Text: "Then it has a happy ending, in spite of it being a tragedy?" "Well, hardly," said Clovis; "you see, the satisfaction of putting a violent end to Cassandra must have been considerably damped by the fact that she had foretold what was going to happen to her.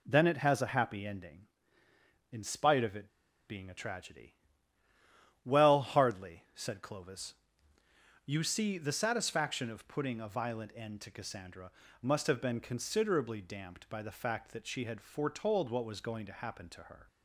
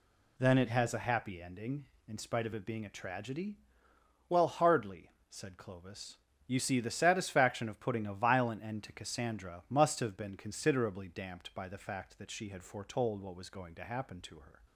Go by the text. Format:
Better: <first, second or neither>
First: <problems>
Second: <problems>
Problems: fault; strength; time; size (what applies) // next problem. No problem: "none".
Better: second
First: pauses between "it" and "being"; at 3.0 s; 0.39 s long // pauses between "Cassandra" and "must"; slight; at 11.7 s; 0.30 s long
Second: none